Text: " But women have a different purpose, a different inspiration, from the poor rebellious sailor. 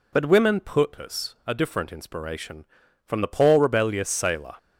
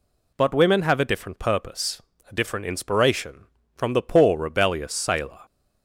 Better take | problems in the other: second | skips "have a different"; at 0.5 s

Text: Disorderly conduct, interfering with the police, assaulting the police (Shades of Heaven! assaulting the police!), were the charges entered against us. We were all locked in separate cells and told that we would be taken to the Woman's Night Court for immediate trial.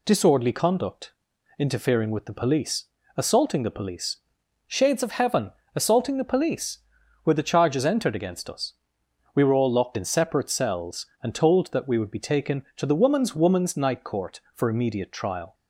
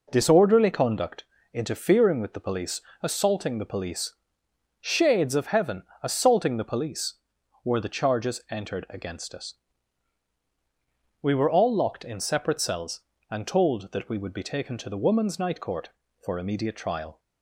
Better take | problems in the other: second | says "Woman's" twice; at 13.3 s

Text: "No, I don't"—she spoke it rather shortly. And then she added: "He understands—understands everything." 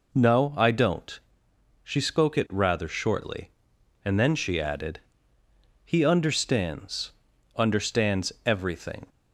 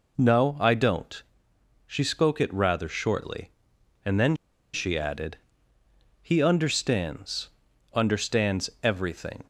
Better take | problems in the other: first | pauses between "then" and "she"; at 4.3 s; 0.37 s long

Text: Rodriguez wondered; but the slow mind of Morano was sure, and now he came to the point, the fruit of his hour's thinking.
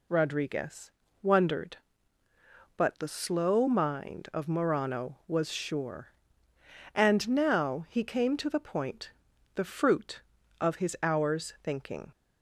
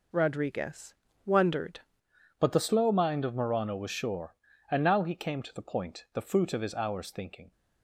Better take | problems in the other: first | pauses between "Rodriguez" and "wondered"; slight; at 0.9 s; 0.32 s long; slight in the first // changes voice at "but"; from 2.4 s on; 5.1 s long

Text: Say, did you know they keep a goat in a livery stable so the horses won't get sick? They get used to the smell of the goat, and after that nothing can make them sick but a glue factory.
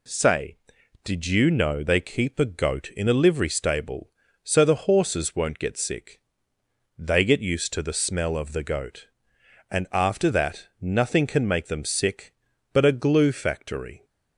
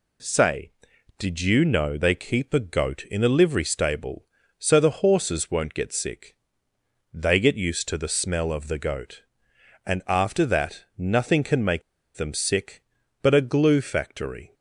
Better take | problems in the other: first | pauses between "make" and "them"; slight; at 11.8 s; 0.35 s long

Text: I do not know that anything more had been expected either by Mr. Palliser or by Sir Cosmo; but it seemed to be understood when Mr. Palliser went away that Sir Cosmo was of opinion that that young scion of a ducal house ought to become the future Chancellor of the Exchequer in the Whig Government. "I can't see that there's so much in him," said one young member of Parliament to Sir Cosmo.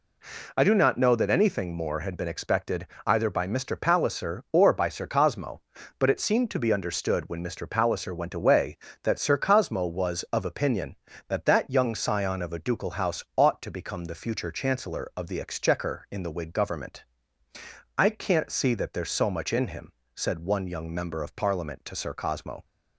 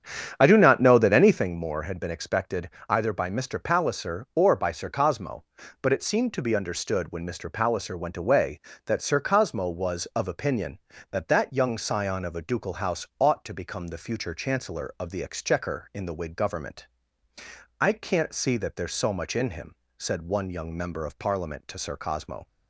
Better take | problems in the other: first | starts louder than the rest; strong; until 1.6 s; 8.5 dB // pauses between "expected" and "either"; slight; at 2.6 s; 0.20 s long; slight in the first

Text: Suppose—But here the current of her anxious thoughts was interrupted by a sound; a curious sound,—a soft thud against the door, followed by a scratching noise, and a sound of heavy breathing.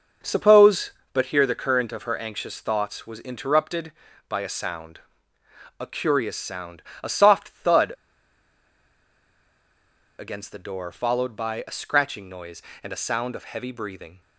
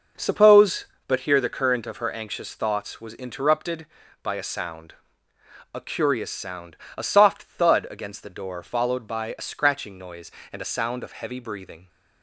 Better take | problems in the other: second | pauses between "thud" and "against"; strong; at 7.9 s; 2.2 s long

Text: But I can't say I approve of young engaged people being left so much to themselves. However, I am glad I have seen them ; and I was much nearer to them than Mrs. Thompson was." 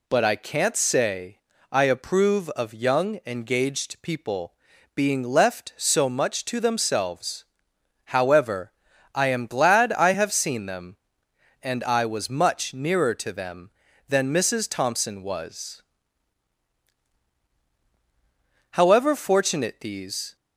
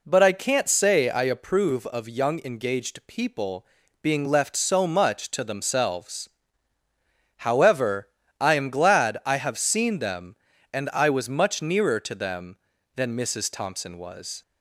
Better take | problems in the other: second | pauses between "say" and "I"; slight; at 1.3 s; 0.34 s long // pauses between "people" and "being"; at 4.5 s; 0.40 s long; slight in the second // goes on to say "However fortunate these"; from 18.7 s on; 1.6 s long

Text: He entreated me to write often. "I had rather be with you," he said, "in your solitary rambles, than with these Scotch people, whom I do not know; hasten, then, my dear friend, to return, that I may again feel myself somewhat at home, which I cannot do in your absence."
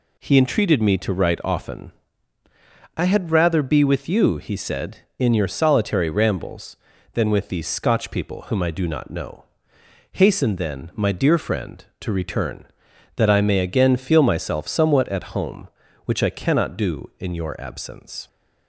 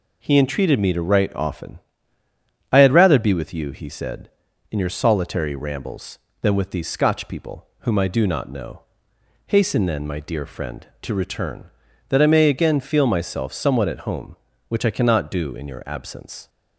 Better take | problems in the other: neither | none

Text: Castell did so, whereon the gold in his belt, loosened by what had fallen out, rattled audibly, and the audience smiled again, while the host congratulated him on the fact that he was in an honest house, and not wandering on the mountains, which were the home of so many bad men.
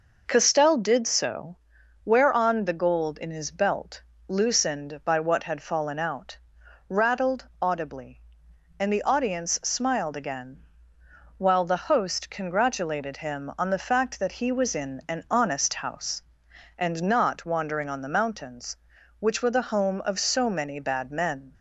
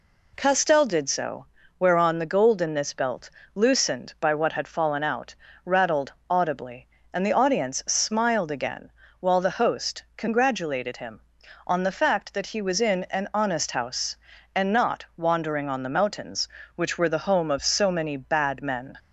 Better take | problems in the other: first | says "this" for "his"; at 2.7 s // pauses between "rattled" and "audibly"; slight; at 6.1 s; 0.16 s long

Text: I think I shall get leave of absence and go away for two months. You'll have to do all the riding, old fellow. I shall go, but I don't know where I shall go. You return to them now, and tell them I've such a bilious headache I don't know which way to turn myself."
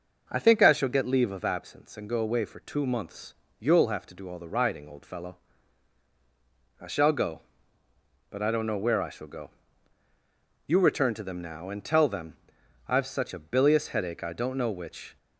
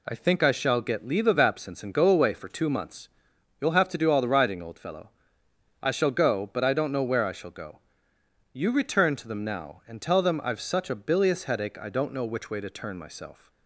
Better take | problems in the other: second | pauses between "them" and "I've"; noticeable; at 12.3 s; 0.54 s long // stops before "way to turn myself"; at 15.1 s

